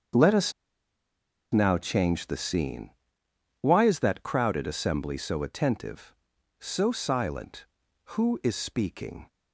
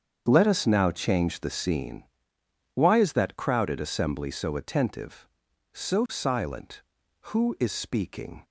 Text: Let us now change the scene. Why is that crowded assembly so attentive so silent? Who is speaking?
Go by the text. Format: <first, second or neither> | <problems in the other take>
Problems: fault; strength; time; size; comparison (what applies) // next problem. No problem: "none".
second | starts louder than the rest; strong; until 2.1 s; 7 dB; strong in the second // pauses between "us" and "now"; at 0.5 s; 1.0 s long